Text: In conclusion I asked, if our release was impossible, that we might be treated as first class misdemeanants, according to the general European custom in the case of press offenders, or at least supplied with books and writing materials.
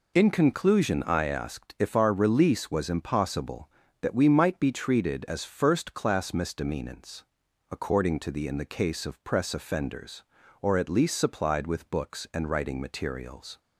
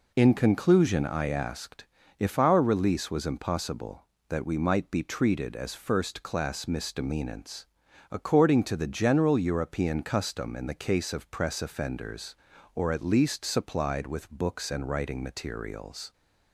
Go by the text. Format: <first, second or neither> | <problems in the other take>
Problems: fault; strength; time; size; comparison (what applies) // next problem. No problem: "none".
second | skips "general European custom"; at 8.4 s